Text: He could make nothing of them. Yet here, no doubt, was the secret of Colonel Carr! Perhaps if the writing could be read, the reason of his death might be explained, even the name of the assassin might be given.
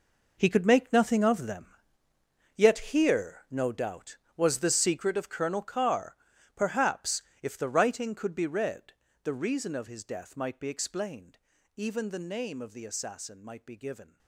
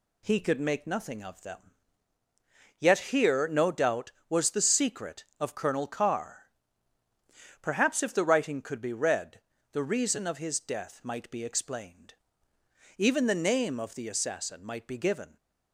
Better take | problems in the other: second | gets quieter; strong; throughout; 15 dB // pauses between "Yet" and "here"; slight; at 2.7 s; 0.16 s long // pauses between "Perhaps" and "if"; slight; at 7.2 s; 0.20 s long

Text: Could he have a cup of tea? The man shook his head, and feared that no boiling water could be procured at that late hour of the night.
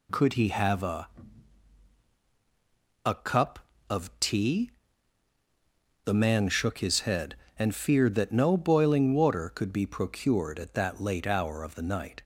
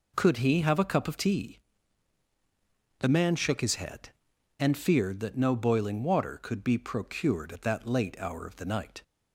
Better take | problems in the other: second | says "a" twice; at 3.0 s

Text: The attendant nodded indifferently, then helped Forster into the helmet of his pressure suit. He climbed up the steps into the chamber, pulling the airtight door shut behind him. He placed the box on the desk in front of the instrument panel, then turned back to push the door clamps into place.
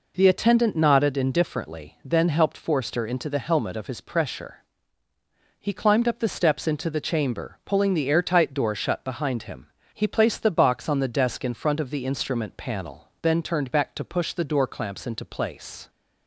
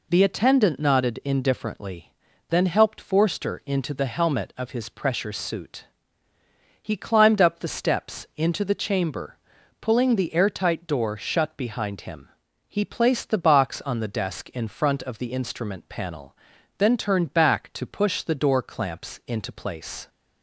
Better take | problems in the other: second | skips "suit"; at 5.1 s

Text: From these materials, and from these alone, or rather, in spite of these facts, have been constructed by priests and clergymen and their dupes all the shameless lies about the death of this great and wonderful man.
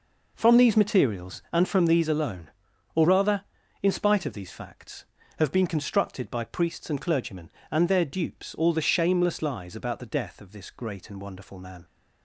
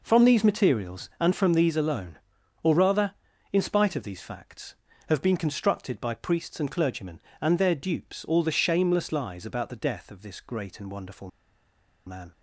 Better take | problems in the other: first | pauses between "wonderful" and "man"; noticeable; at 11.2 s; 0.77 s long

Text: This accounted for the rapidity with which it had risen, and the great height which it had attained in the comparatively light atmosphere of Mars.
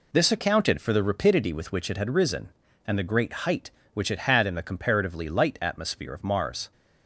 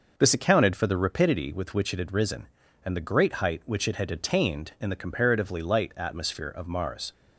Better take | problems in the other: second | pauses between "great" and "height"; slight; at 3.3 s; 0.16 s long // skips "attained"; at 4.4 s

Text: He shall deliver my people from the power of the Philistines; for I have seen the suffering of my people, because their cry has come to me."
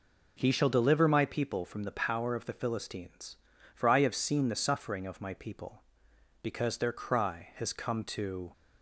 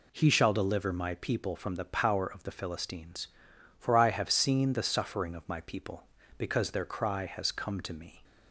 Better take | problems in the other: second | stops before "me"; at 8.5 s

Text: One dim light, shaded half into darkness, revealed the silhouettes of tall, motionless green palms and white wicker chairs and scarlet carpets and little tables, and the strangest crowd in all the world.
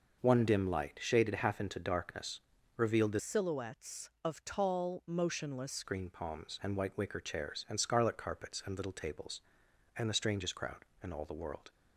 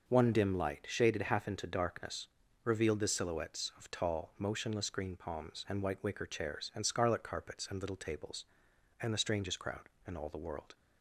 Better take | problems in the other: second | changes voice from "silhouettes" to "motionless"; from 3.1 to 5.8 s; 2.7 s long

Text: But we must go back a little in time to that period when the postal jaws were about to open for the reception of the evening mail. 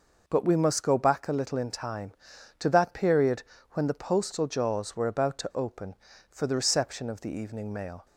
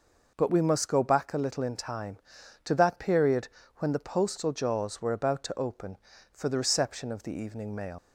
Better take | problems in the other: first | pauses between "period" and "when"; slight; at 3.4 s; 0.30 s long; slight in the first // leaves "mail" unfinished; at 7.9 s; 85 ms

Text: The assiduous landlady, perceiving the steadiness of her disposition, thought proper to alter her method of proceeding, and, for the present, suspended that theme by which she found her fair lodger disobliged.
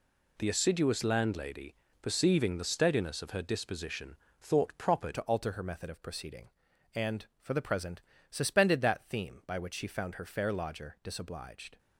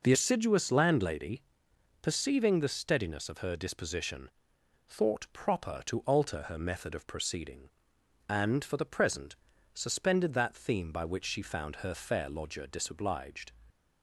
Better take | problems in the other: second | changes voice at "to"; from 5.1 s on; 6.6 s long

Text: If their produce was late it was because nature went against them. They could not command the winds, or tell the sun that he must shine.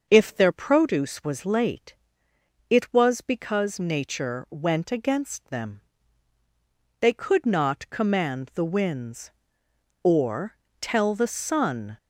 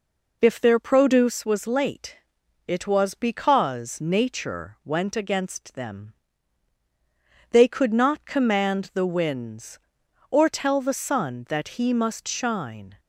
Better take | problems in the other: second | starts louder than the rest; until 1.0 s; 6 dB // pauses between "late" and "it"; noticeable; at 1.9 s; 0.76 s long; noticeable in the second // pauses between "or" and "tell"; slight; at 10.5 s; 0.24 s long // stops before "that he must shine"; at 11.9 s

